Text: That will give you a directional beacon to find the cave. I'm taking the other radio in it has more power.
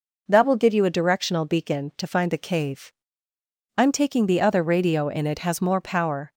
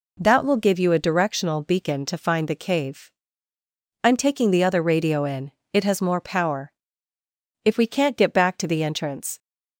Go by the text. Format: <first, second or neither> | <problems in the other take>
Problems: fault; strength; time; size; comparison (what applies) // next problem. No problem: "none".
first | pauses between "in" and "it"; slight; at 5.5 s; 0.20 s long // goes on to say "If we can't get back to the entrance"; strong; from 7.6 s on; 1.7 s long